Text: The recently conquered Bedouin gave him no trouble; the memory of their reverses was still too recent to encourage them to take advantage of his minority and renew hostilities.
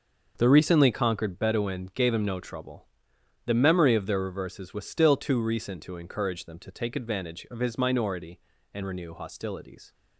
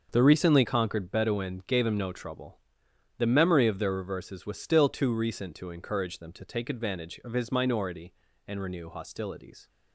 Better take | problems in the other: neither | starts louder than the rest; the same in both

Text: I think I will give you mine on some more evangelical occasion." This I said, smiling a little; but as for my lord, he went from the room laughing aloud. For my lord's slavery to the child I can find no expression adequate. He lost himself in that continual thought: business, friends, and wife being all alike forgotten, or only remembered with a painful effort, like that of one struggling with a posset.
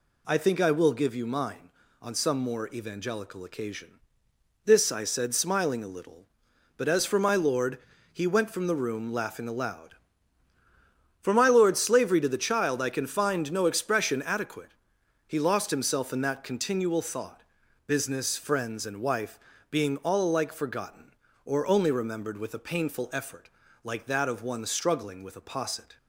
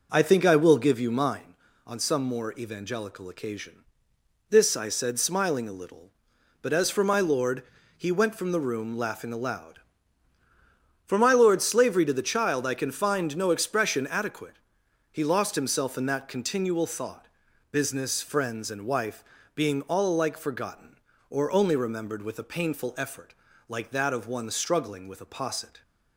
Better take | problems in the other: first | starts louder than the rest; noticeable; until 1.4 s; 4.5 dB // pauses between "wife" and "being"; slight; at 19.2 s; 0.32 s long; slight in the first

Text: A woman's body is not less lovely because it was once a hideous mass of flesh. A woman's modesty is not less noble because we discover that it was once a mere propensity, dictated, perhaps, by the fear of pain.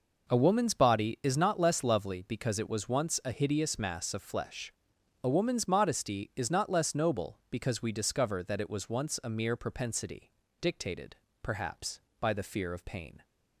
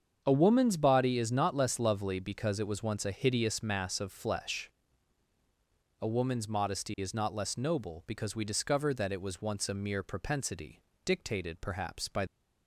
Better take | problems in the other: first | starts louder than the rest; strong; until 1.2 s; 7 dB // stops before "the fear of pain"; at 12.2 s

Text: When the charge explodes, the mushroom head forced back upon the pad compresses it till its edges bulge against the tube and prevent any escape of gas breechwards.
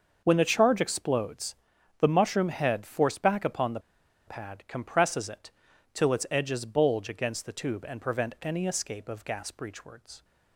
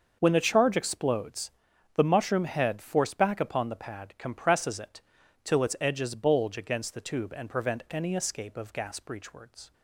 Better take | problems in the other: second | starts louder than the rest; until 1.2 s; 6.5 dB; also in the second // pauses between "the" and "pad"; noticeable; at 3.7 s; 0.48 s long // pauses between "it" and "till"; at 5.5 s; 0.42 s long; also in the second

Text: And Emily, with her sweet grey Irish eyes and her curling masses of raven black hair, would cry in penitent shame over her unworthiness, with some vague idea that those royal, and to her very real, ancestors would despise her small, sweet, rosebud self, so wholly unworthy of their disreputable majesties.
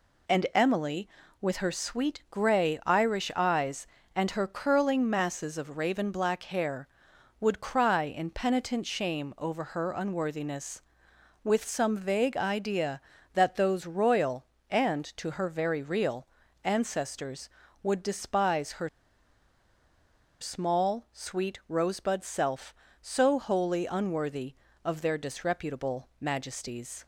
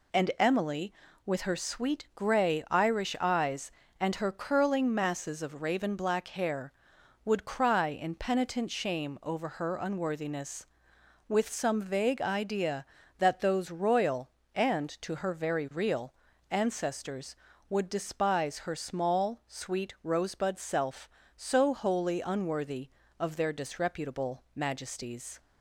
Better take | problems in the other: second | pauses between "her" and "small"; strong; at 18.8 s; 1.5 s long

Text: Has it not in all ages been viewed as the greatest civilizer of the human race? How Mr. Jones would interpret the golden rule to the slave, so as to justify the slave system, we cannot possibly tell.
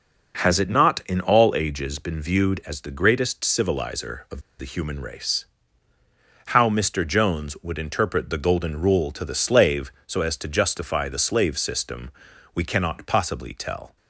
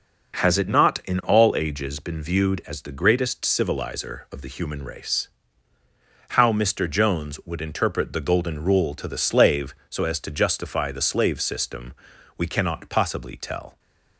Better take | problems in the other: second | pauses between "of" and "the"; slight; at 4.4 s; 0.18 s long

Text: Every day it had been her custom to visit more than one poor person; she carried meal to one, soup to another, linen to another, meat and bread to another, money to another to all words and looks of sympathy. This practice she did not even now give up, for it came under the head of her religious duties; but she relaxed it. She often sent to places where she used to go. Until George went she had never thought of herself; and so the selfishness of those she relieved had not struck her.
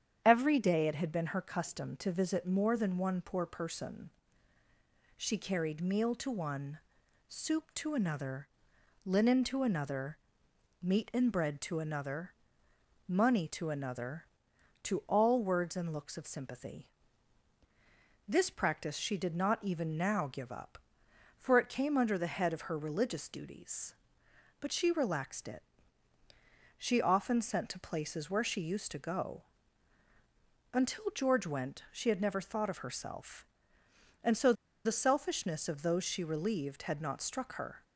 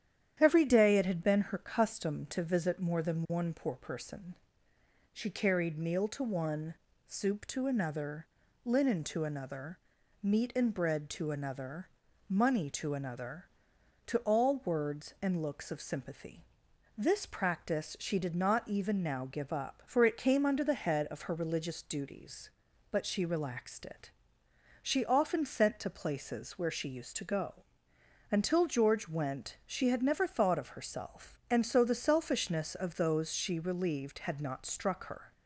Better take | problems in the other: second | starts louder than the rest; strong; until 1.2 s; 8.5 dB; strong in the second // pauses between "so" and "the"; slight; at 34.5 s; 0.31 s long

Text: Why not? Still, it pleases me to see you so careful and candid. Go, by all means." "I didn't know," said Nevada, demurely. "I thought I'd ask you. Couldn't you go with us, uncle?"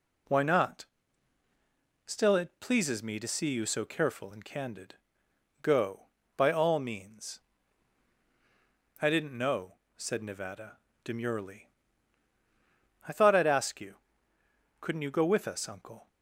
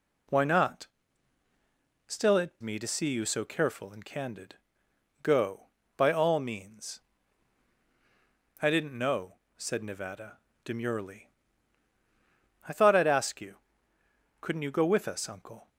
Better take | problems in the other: first | skips "pleases"; at 2.6 s

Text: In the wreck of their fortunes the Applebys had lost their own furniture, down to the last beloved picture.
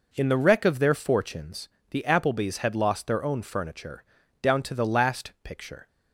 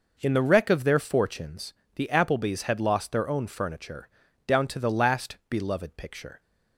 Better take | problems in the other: second | pauses between "fortunes" and "the"; slight; at 1.6 s; 0.22 s long; slight in the second // skips "beloved"; at 5.3 s

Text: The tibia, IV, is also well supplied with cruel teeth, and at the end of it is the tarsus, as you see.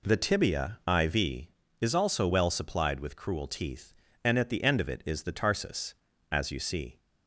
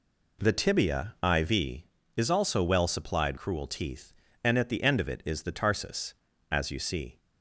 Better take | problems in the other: first | skips "with"; at 3.3 s

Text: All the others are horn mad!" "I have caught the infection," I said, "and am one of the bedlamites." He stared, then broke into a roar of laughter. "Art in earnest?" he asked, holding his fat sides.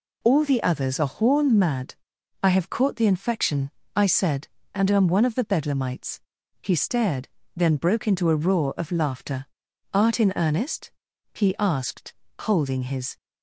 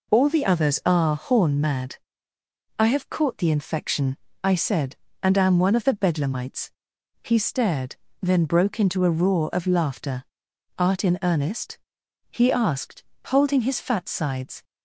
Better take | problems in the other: second | stops before "fat sides"; at 13.1 s

